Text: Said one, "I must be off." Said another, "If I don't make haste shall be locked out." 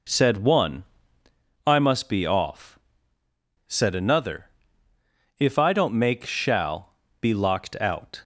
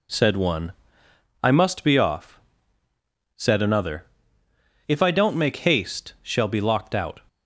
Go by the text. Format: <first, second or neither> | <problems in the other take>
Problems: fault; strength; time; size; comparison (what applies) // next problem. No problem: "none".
second | skips "haste"; at 6.2 s // pauses between "shall" and "be"; slight; at 6.9 s; 0.26 s long